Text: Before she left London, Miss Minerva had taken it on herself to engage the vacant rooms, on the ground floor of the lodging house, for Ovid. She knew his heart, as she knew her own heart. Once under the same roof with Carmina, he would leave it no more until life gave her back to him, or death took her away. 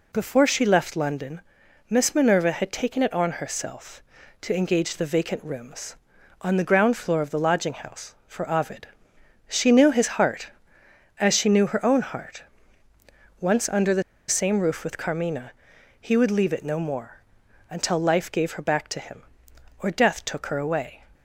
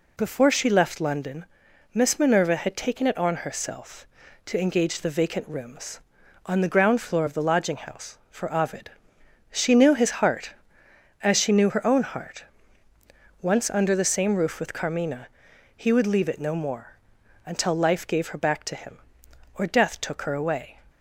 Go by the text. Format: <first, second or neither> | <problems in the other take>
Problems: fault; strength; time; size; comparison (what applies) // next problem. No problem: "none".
second | pauses between "the" and "same"; slight; at 14.0 s; 0.27 s long // pauses between "more" and "until"; noticeable; at 17.2 s; 0.48 s long; noticeable in the second